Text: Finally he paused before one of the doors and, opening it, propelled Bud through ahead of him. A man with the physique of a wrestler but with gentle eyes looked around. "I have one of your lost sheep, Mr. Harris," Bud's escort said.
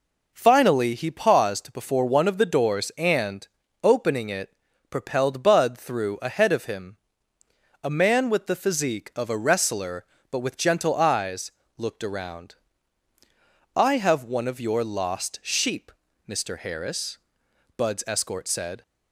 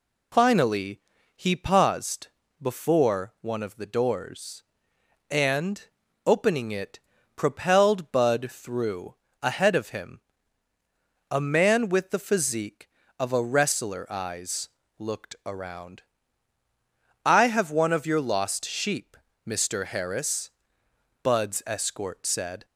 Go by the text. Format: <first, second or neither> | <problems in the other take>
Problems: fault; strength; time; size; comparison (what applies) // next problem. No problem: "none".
first | pauses between "Finally" and "he"; slight; at 0.9 s; 0.36 s long // pauses between "paused" and "before"; slight; at 2.2 s; 0.30 s long // pauses between "through" and "ahead"; slight; at 9.1 s; 0.30 s long // skips "but with gentle"; at 14.1 s // pauses between "eyes" and "looked"; slight; at 14.6 s; 0.28 s long; slight in the first